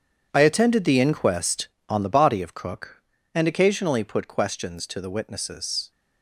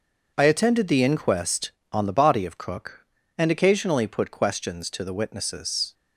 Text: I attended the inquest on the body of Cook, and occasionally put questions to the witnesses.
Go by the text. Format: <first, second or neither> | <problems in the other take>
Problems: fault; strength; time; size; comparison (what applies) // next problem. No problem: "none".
second | gets quieter; strong; throughout; 12 dB